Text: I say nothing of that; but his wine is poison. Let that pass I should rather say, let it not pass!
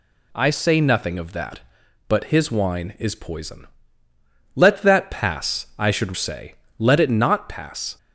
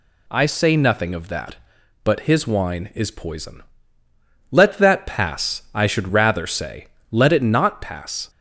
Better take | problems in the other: second | skips "rather"; at 6.1 s

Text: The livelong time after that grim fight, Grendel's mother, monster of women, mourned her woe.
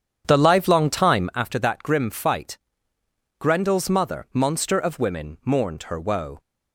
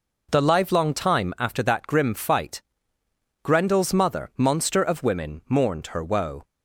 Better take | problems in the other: second | starts louder than the rest; strong; until 1.5 s; 8.5 dB

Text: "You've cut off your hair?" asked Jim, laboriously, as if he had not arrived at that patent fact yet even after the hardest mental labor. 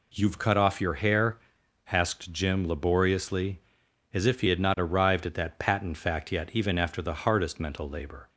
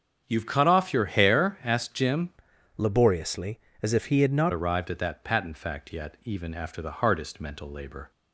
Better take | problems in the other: first | starts louder than the rest; strong; until 1.2 s; 7.5 dB // changes voice from "laboriously" to "not"; from 2.7 to 4.5 s; 1.8 s long

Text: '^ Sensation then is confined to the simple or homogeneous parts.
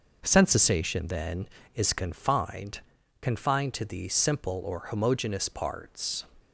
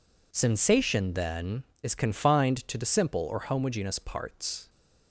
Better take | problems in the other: second | says "confined" twice; at 3.2 s

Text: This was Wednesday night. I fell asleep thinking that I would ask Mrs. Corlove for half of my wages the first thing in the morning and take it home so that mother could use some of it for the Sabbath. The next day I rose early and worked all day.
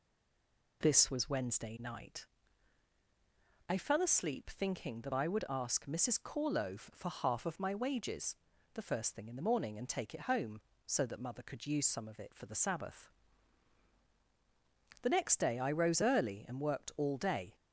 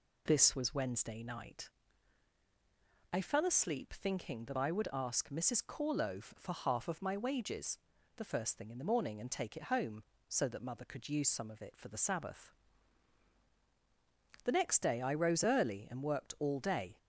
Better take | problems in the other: second | stays silent before the first word; slight; until 0.8 s; 0.8 s long // pauses between "wages" and "the"; at 8.3 s; 0.38 s long; also in the second

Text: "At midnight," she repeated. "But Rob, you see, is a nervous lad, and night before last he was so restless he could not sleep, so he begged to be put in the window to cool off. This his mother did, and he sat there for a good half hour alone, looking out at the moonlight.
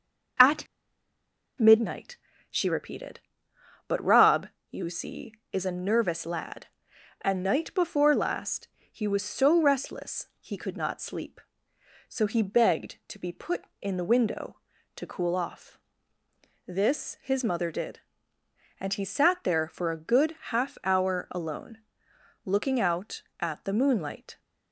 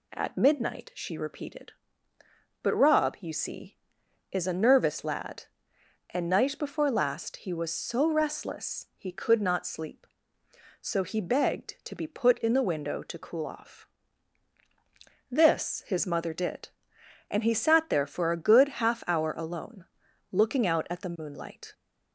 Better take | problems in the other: second | pauses between "At" and "midnight"; noticeable; at 0.6 s; 0.94 s long // pauses between "last" and "he"; slight; at 8.6 s; 0.24 s long

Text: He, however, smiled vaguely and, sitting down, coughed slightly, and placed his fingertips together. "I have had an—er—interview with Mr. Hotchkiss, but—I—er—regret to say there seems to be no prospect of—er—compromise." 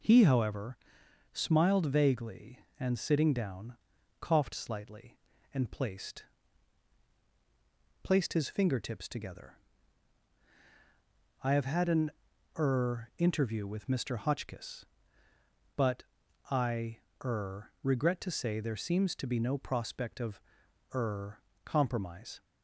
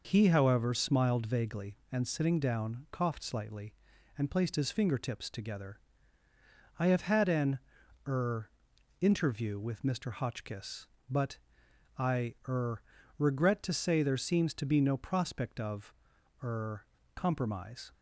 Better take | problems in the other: second | says "placed" twice; at 8.0 s

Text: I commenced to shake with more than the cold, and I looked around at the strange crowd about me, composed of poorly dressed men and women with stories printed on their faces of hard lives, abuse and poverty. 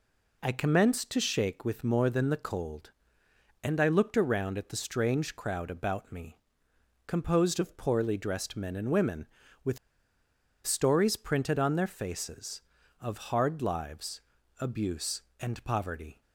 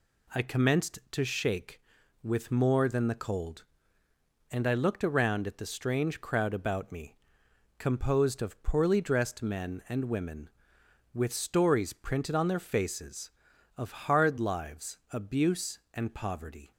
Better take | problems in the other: second | pauses between "with" and "stories"; noticeable; at 9.7 s; 0.88 s long

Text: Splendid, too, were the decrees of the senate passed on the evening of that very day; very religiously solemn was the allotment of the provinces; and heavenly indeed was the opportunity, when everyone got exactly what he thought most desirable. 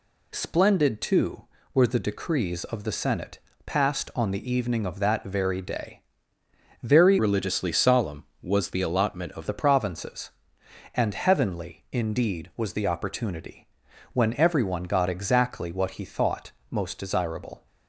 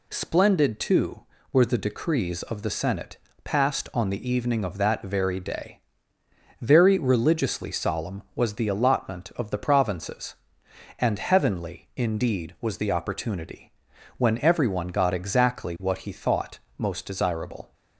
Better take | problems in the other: second | pauses between "senate" and "passed"; slight; at 3.3 s; 0.26 s long; slight in the second // changes voice from "religiously" to "of"; from 7.1 to 9.4 s; 2.3 s long // pauses between "thought" and "most"; slight; at 16.5 s; 0.20 s long; slight in the second

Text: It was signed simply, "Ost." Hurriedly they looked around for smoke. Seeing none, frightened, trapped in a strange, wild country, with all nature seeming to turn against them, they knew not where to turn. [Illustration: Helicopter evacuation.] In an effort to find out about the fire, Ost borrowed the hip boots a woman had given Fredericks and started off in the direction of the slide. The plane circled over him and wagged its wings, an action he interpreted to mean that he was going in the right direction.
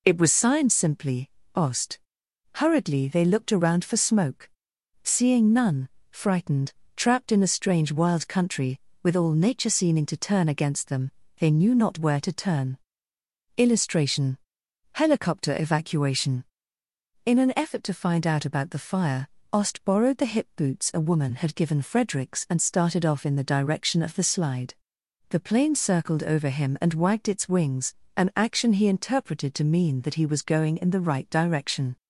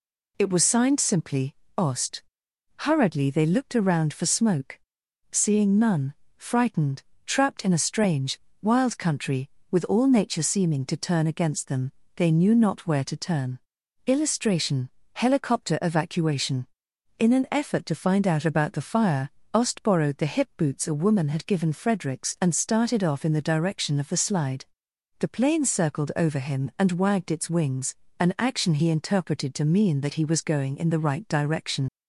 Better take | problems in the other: first | leaves "direction" unfinished; at 31.8 s; 60 ms

